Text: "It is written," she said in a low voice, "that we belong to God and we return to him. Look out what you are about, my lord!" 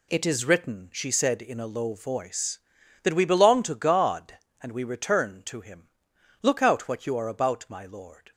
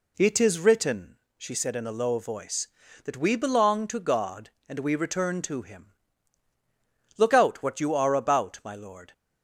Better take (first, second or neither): neither